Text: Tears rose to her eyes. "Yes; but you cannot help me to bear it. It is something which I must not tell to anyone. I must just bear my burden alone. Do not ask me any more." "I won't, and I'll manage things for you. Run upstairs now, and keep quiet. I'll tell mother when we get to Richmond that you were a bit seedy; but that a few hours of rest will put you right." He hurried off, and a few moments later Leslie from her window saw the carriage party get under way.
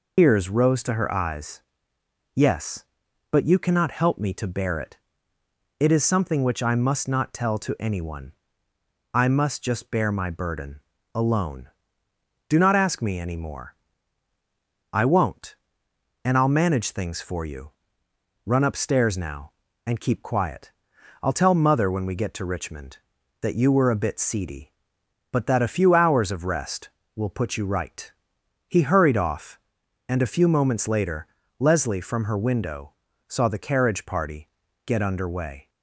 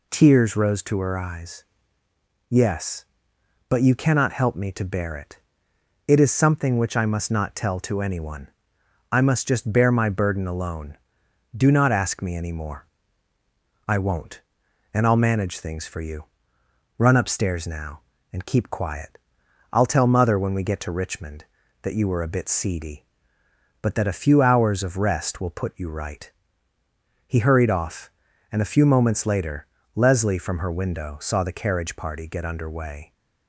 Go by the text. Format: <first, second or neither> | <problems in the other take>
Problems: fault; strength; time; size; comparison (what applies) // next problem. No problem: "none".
second | loses the start of "Tears"; at 0.1 s; 150 ms // pauses between "burden" and "alone"; slight; at 10.7 s; 0.34 s long // pauses between "later" and "Leslie"; slight; at 31.2 s; 0.32 s long; slight in the second // pauses between "window" and "saw"; slight; at 32.9 s; 0.36 s long // pauses between "party" and "get"; slight; at 34.4 s; 0.36 s long